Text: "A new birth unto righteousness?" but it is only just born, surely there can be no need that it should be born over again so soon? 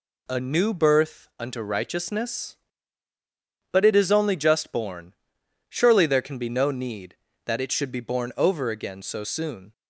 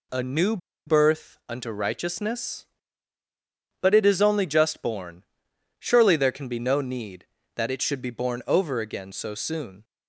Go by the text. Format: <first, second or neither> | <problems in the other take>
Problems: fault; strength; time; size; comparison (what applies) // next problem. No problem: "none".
first | pauses between "new" and "birth"; slight; at 0.5 s; 0.29 s long